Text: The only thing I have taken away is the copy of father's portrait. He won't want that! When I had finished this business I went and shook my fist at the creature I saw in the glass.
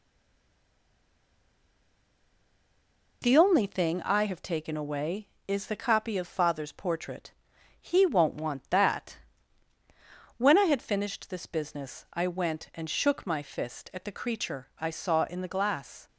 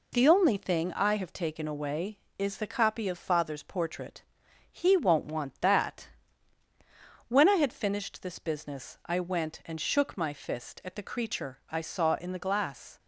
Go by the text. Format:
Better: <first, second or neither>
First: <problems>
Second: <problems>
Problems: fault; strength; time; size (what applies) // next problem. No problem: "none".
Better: second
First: stays silent before the first word; strong; until 3.2 s; 3.2 s long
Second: none